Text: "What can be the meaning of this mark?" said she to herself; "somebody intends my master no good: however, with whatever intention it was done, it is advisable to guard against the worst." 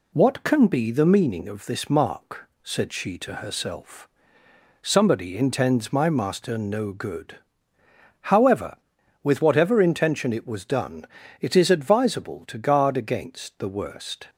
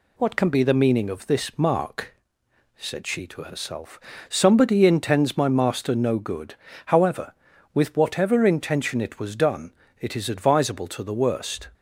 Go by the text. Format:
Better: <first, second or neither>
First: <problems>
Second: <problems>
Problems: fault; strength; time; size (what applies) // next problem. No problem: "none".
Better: first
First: none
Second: skips "guard against"; at 11.0 s